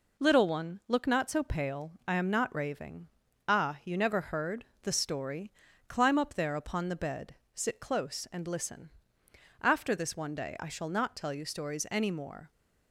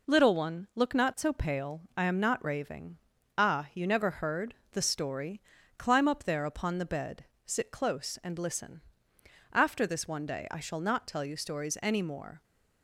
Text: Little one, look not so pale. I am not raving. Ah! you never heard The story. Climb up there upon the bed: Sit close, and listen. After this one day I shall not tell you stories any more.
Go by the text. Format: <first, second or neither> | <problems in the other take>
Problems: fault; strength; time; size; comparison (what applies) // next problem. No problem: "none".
neither | pauses between "heard" and "The"; slight; the same in both